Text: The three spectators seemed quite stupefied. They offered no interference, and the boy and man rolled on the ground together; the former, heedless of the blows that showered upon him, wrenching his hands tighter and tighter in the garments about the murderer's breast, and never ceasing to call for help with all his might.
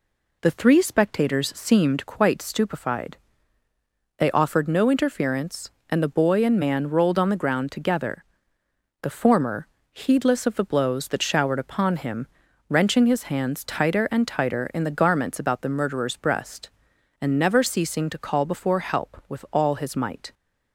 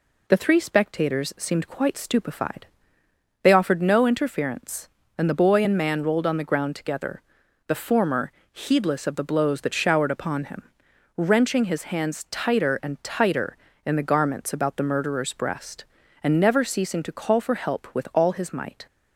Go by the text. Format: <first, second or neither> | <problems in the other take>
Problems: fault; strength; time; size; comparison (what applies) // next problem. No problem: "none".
second | says "before" for "for"; at 18.4 s